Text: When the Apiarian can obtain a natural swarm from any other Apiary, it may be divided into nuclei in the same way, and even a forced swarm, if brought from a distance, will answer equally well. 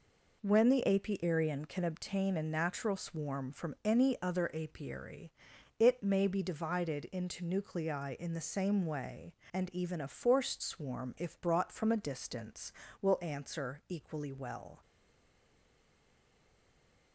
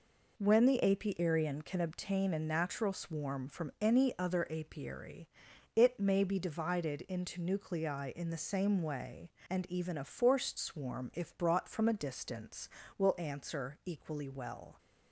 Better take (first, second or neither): second